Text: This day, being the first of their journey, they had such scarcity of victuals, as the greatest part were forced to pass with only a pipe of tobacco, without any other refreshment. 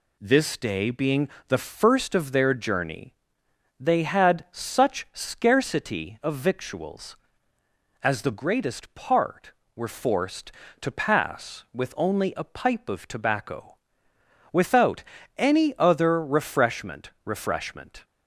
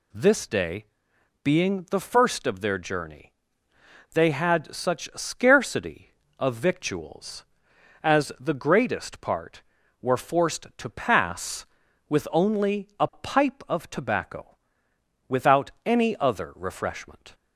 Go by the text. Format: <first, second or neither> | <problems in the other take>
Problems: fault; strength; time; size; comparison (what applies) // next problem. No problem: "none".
second | pauses between "being" and "the"; slight; at 1.2 s; 0.20 s long // pauses between "without" and "any"; slight; at 15.0 s; 0.34 s long // says "refreshment" twice; at 17.2 s